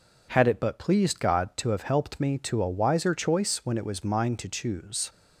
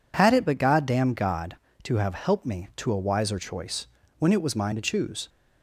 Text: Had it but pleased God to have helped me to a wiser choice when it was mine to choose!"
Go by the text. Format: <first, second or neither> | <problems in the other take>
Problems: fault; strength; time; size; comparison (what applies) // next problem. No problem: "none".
first | says "goddamn" for "pleased"; at 0.5 s // pauses between "choice" and "when"; slight; at 3.8 s; 0.32 s long